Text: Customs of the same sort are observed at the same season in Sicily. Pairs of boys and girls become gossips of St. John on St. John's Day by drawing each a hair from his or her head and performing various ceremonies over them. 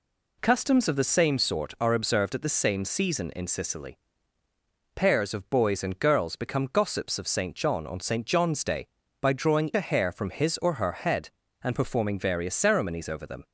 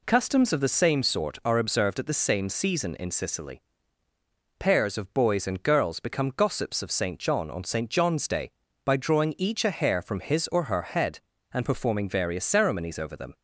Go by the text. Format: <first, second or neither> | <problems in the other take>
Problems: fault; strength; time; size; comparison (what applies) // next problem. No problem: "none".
second | skips "each"; at 9.7 s